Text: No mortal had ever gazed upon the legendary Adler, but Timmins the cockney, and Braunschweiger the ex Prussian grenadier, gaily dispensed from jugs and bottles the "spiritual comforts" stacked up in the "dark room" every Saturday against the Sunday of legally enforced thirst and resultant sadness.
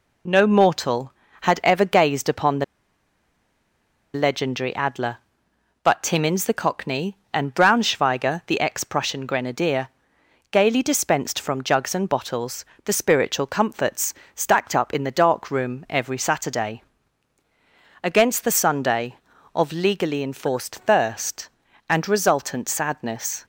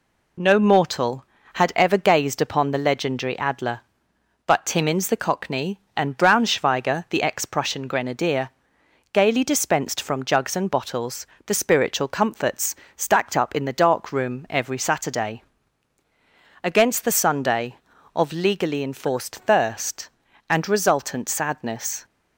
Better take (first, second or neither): second